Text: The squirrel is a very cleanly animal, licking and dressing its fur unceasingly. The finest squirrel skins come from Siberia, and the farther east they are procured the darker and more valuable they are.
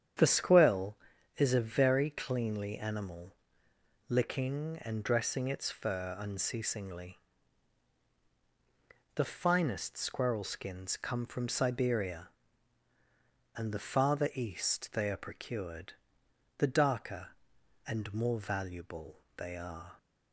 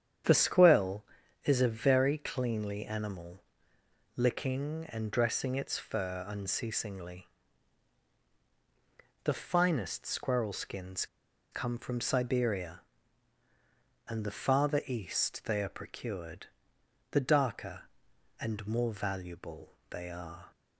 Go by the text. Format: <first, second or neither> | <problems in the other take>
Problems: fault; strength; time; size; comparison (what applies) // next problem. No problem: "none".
first | starts louder than the rest; strong; until 1.6 s; 9 dB; strong in the first // pauses between "skins" and "come"; noticeable; at 11.0 s; 0.46 s long // pauses between "procured" and "the"; noticeable; at 16.4 s; 0.66 s long; noticeable in the first // pauses between "valuable" and "they"; slight; at 19.7 s; 0.16 s long; slight in the first